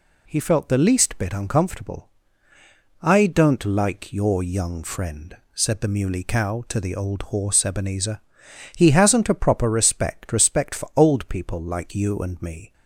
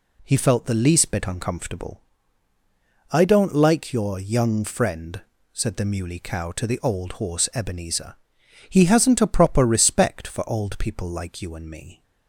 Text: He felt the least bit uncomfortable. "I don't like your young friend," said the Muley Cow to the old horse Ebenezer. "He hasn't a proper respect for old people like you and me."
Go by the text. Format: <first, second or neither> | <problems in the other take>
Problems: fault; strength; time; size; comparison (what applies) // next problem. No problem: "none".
second | says "respect" twice; at 10.3 s